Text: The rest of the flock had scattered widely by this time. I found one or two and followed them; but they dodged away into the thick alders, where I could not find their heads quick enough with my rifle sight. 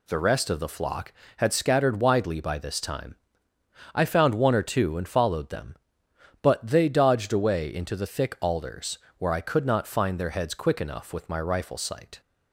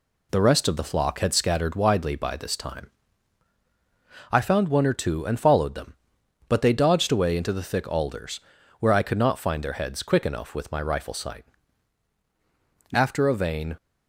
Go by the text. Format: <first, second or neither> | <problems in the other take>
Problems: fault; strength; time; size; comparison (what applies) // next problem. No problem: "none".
first | goes on to say "After a vain"; noticeable; from 12.9 s on; 0.82 s long